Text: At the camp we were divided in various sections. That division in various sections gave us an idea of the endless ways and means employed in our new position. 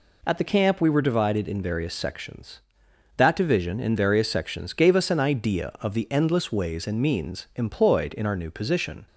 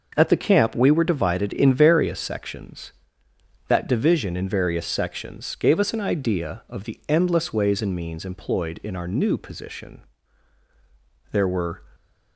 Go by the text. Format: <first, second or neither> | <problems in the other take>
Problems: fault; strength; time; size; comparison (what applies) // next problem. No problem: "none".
first | goes on to say "There were"; from 11.3 s on; 0.50 s long